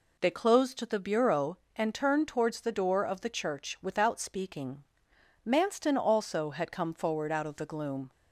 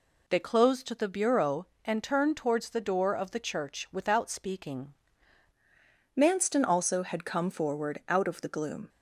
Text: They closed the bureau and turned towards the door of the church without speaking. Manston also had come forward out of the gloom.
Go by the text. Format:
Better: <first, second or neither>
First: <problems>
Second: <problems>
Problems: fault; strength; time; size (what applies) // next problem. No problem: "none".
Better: first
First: none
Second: changes voice at "Manston"; from 6.1 s on; 2.7 s long